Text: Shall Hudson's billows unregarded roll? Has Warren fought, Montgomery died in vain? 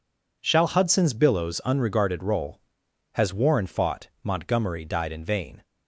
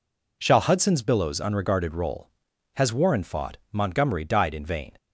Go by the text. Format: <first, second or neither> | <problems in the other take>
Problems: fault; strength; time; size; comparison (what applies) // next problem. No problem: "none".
neither | none